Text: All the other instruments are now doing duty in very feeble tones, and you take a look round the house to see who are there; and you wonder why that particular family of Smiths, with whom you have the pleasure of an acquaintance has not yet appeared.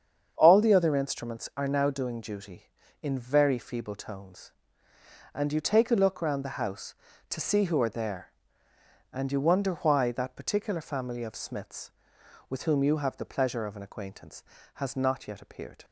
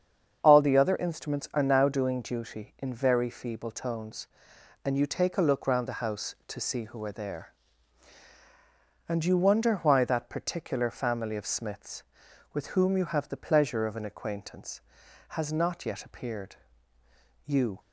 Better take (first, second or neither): first